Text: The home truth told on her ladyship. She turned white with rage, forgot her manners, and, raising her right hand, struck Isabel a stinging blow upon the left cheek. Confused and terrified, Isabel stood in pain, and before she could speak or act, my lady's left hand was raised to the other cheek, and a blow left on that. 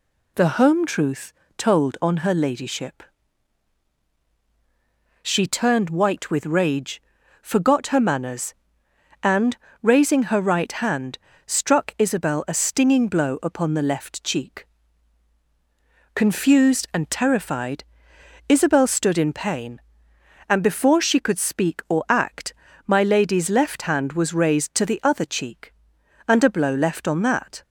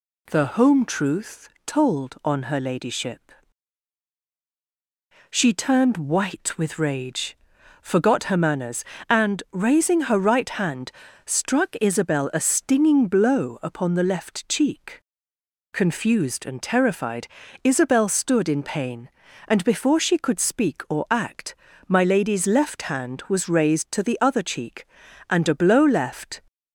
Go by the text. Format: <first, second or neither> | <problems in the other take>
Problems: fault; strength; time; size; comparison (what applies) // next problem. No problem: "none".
first | pauses between "truth" and "told"; slight; at 1.4 s; 0.18 s long; slight in the first // stops before "on that"; at 26.4 s